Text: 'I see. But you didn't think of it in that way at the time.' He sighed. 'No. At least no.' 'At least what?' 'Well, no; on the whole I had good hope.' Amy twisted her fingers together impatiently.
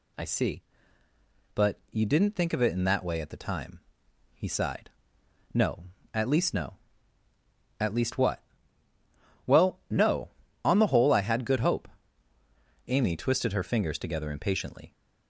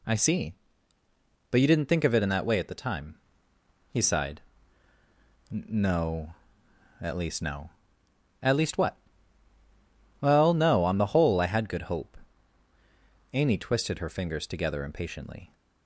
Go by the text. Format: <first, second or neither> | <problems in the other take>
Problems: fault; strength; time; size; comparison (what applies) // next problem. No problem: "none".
neither | none